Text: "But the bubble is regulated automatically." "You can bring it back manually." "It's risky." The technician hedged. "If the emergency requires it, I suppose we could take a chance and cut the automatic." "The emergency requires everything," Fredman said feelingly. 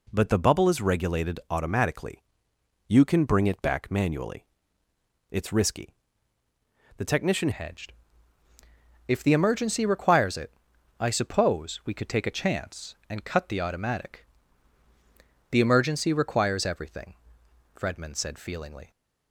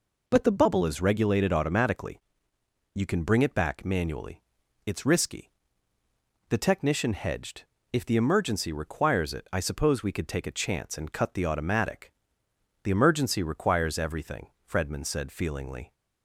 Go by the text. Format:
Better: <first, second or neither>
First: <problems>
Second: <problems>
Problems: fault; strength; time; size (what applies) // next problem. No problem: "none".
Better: second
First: changes voice at "hedged"; from 7.5 s on; 11.4 s long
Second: none